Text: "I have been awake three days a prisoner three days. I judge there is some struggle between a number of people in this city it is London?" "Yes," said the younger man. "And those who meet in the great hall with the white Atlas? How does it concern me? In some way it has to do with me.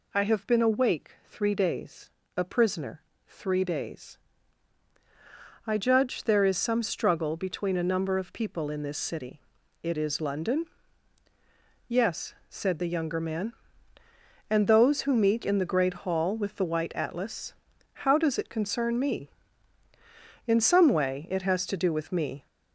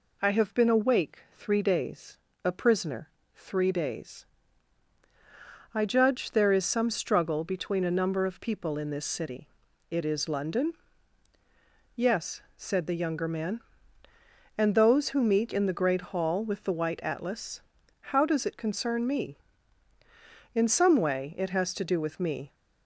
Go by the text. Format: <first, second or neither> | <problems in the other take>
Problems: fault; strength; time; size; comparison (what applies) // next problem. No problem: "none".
second | gets louder; noticeable; throughout; 4.5 dB // pauses between "awake" and "three"; slight; at 1.1 s; 0.16 s long; slight in the second // pauses between "days" and "a"; slight; at 2.1 s; 0.26 s long; slight in the second // pauses between "prisoner" and "three"; slight; at 3.0 s; 0.24 s long; slight in the second // pauses between "city" and "it"; at 9.4 s; 0.40 s long; also in the second